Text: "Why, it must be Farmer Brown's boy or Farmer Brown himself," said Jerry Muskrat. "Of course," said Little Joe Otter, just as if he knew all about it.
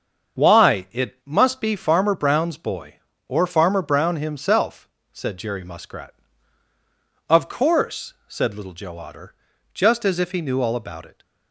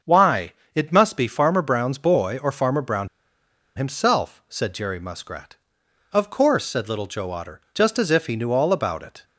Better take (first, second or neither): first